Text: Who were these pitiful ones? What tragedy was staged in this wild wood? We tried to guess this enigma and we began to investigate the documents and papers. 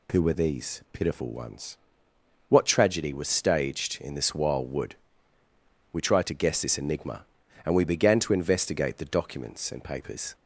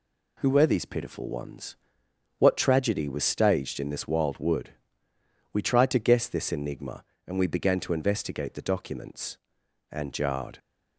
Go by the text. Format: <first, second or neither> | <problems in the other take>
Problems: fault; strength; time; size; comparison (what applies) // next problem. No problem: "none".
first | says "jarred" for "papers"; at 10.1 s